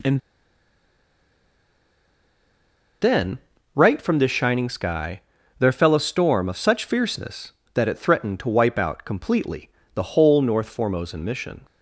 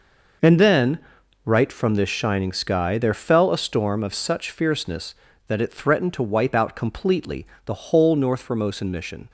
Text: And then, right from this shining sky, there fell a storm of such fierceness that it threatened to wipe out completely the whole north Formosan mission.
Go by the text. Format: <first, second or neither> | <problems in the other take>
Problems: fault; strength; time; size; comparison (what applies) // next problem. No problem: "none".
second | pauses between "And" and "then"; strong; at 0.1 s; 2.8 s long // pauses between "completely" and "the"; slight; at 9.6 s; 0.26 s long; slight in the second